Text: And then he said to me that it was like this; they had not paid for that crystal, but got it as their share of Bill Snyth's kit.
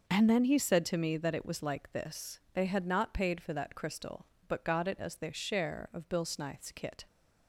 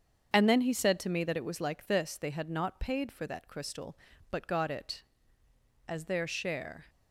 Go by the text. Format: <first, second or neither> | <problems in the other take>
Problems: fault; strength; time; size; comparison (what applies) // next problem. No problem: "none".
first | starts louder than the rest; strong; until 1.3 s; 7.5 dB; noticeable in the first // stops before "of Bill Snyth's kit"; at 6.8 s